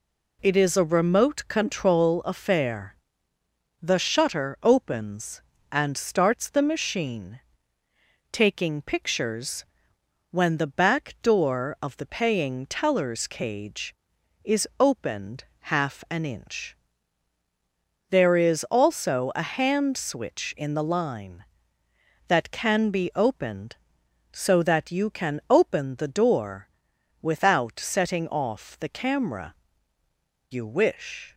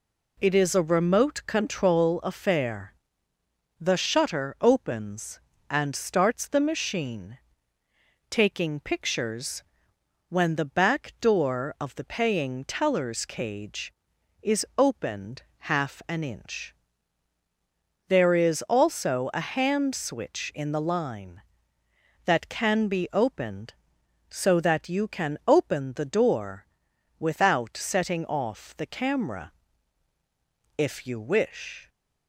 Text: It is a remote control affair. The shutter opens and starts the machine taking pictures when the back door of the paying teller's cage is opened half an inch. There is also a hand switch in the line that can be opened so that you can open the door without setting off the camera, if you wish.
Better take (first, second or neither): second